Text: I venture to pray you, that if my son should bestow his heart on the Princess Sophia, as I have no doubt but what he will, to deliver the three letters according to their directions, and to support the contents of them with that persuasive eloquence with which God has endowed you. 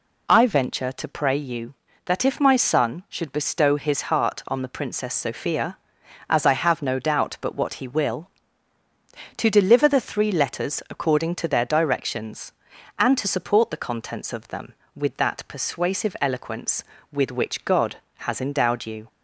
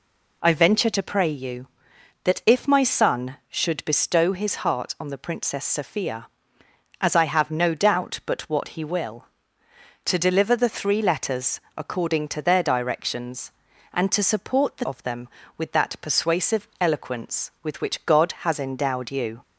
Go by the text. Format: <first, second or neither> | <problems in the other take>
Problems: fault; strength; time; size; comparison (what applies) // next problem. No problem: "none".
first | pauses between "letters" and "according"; slight; at 11.5 s; 0.16 s long // skips "contents"; at 14.8 s